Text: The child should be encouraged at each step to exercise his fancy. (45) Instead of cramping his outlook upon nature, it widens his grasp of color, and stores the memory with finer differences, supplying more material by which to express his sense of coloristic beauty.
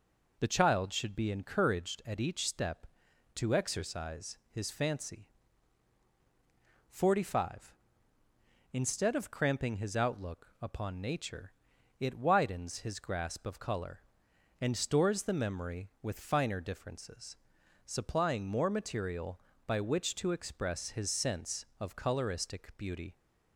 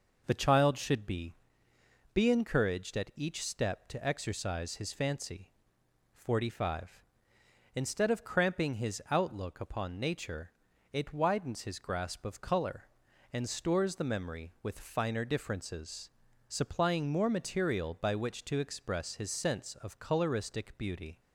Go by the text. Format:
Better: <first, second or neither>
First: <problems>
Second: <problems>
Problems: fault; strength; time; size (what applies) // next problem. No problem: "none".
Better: first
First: none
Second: says "be" twice; at 2.1 s